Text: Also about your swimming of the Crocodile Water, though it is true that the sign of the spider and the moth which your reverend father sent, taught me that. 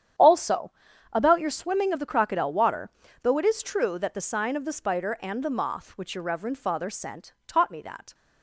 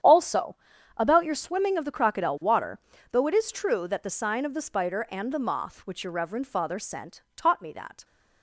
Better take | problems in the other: neither | starts louder than the rest; strong; the same in both // pauses between "Also" and "about"; the same in both

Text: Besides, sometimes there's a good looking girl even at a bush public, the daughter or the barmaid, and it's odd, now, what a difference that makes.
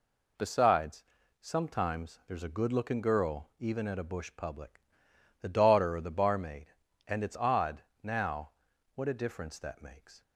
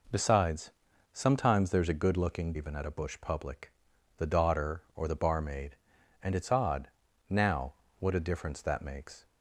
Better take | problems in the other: first | skips "girl"; at 2.5 s

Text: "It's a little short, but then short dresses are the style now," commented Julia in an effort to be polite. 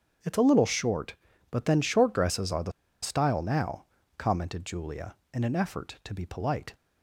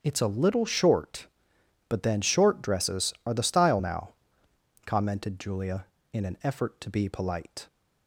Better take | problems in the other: second | starts louder than the rest; until 1.5 s; 6.5 dB; strong in the second // pauses between "the" and "style"; slight; at 2.7 s; 0.31 s long

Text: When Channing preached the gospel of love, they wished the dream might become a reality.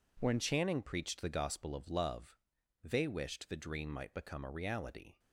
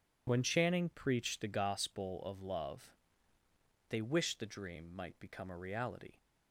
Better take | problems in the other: second | changes voice at "Channing"; from 0.3 s on; 4.8 s long

